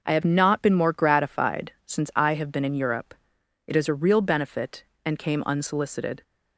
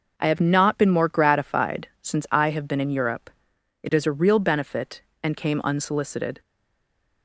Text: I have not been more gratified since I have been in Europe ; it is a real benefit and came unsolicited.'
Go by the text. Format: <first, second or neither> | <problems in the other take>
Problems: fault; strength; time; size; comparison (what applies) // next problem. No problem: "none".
first | stays silent after the last word; slight; from 6.4 s on; 0.8 s long